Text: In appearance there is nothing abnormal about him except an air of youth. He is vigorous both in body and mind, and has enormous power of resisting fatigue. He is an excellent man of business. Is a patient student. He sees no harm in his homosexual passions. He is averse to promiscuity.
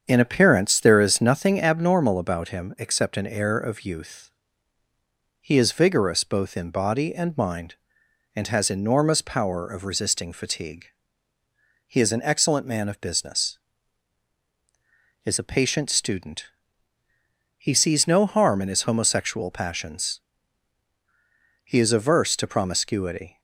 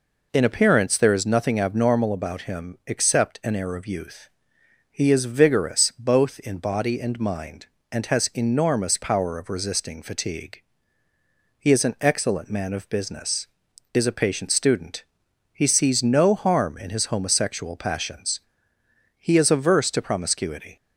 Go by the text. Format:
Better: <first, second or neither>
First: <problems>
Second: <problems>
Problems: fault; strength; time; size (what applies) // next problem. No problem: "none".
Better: second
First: starts louder than the rest; strong; until 1.5 s; 7.5 dB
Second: none